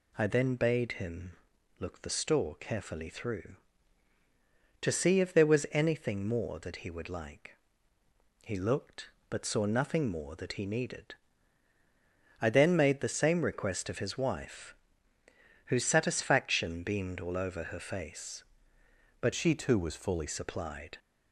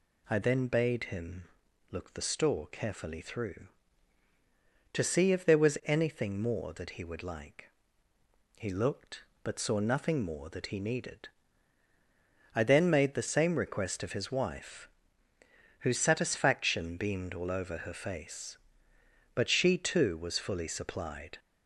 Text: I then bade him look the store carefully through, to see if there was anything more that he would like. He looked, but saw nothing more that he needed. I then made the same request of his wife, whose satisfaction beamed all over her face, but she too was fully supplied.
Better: second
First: pauses between "him" and "look"; noticeable; at 1.3 s; 0.46 s long // changes voice from "she" to "fully"; from 19.3 to 20.2 s; 0.9 s long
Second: pauses between "him" and "look"; noticeable; at 1.4 s; 0.46 s long

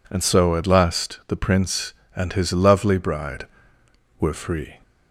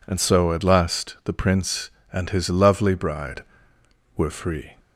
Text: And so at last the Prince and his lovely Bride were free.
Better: neither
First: none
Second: none

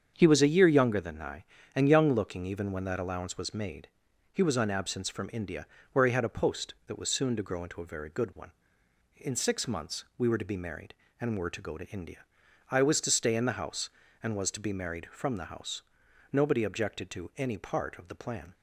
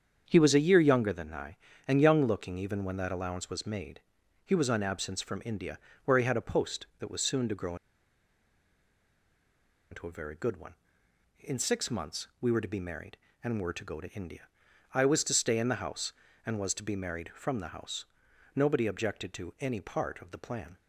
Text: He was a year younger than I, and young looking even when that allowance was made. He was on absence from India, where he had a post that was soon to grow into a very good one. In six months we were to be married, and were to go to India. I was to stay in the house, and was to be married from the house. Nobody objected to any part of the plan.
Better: first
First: starts louder than the rest; strong; until 1.1 s; 7.5 dB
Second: starts louder than the rest; strong; until 1.2 s; 7.5 dB // pauses between "grow" and "into"; strong; at 7.7 s; 2.1 s long

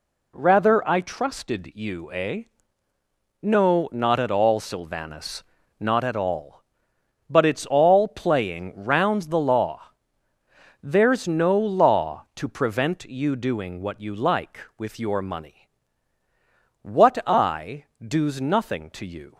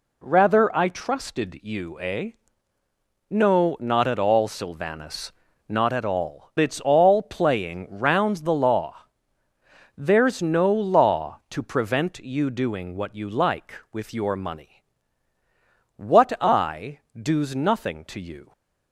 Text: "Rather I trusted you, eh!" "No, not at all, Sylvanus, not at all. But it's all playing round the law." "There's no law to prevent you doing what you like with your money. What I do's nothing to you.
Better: first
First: pauses between "I" and "do's"; slight; at 17.8 s; 0.16 s long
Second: skips "But"; at 6.5 s // pauses between "I" and "do's"; slight; at 16.9 s; 0.16 s long

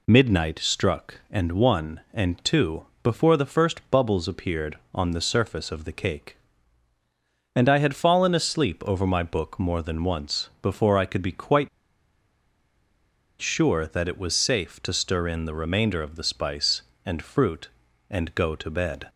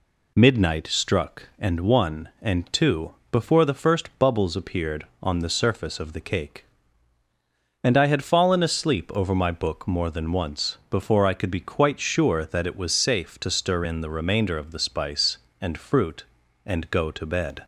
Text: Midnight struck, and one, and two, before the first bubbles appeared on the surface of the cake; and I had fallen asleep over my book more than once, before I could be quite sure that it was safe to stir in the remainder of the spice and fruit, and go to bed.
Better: second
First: pauses between "quite" and "sure"; strong; at 11.6 s; 1.7 s long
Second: none

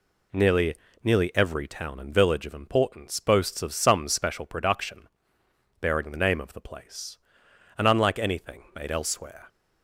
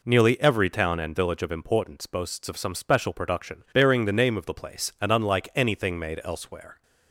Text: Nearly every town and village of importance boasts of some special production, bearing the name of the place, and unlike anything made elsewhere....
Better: second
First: says "Nearly" twice; at 1.0 s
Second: none

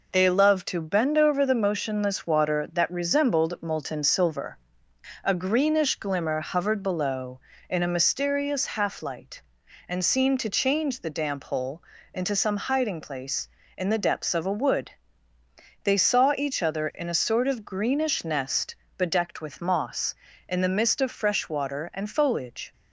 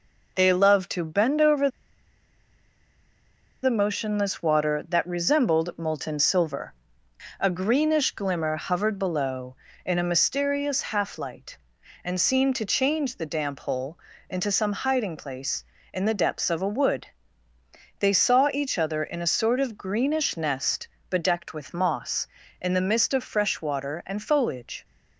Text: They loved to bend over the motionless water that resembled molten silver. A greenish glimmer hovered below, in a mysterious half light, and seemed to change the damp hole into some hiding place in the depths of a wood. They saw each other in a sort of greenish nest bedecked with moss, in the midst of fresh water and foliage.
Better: first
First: pauses between "hole" and "into"; slight; at 11.8 s; 0.32 s long // pauses between "nest" and "bedecked"; slight; at 18.7 s; 0.20 s long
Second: pauses between "over" and "the"; strong; at 1.6 s; 1.9 s long // pauses between "hole" and "into"; slight; at 13.9 s; 0.32 s long // pauses between "nest" and "bedecked"; slight; at 20.8 s; 0.20 s long

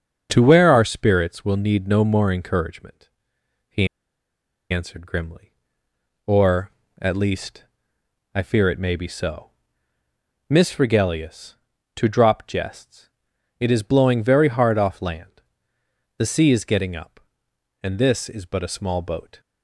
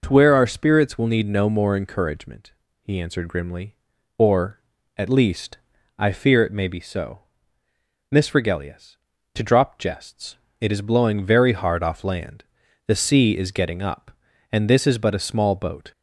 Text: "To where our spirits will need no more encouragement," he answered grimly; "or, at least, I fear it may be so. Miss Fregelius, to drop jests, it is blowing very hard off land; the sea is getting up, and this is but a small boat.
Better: second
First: starts louder than the rest; until 1.3 s; 7 dB // pauses between "he" and "answered"; noticeable; at 3.8 s; 0.85 s long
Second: none

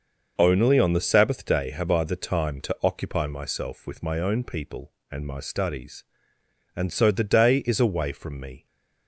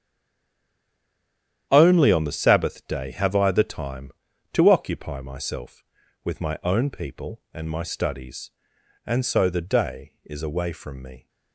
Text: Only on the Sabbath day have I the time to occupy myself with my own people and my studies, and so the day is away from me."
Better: first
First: starts louder than the rest; until 1.3 s; 6 dB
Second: stays silent before the first word; noticeable; until 1.6 s; 1.6 s long // starts louder than the rest; strong; until 2.7 s; 10 dB

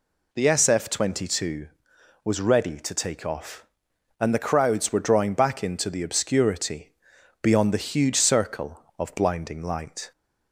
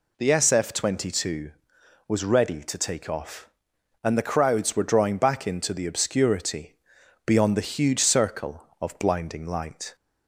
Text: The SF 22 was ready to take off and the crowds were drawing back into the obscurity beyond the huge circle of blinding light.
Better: neither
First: pauses between "obscurity" and "beyond"; noticeable; at 6.9 s; 0.50 s long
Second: pauses between "obscurity" and "beyond"; noticeable; at 6.7 s; 0.50 s long

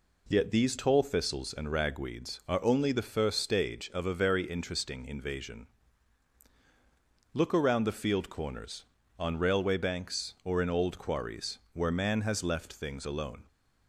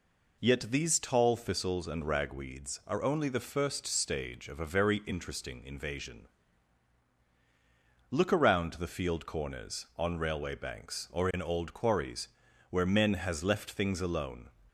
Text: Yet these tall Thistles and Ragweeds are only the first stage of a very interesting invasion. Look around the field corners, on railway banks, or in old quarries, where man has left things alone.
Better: first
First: none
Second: says "men" for "man"; at 12.8 s

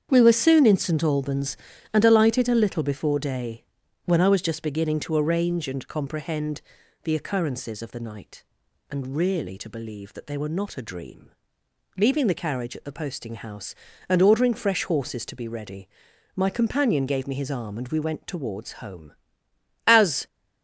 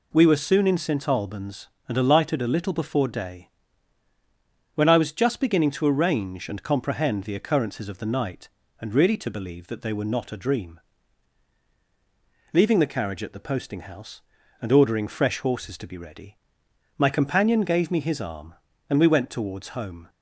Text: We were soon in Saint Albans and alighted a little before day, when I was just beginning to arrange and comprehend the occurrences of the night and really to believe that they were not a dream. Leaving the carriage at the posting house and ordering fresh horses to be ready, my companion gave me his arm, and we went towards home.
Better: second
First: starts louder than the rest; strong; until 1.1 s; 8 dB // pauses between "comprehend" and "the"; at 6.6 s; 0.42 s long // goes on to say "As"; slight; from 19.8 s on; 0.40 s long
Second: none

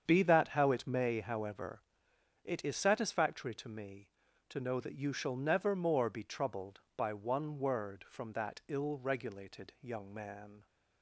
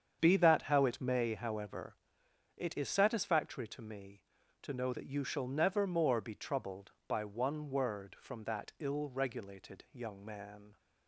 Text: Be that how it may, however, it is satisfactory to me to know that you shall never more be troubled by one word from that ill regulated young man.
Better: neither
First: starts louder than the rest; strong; until 1.0 s; 7.5 dB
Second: starts louder than the rest; strong; until 1.2 s; 7.5 dB

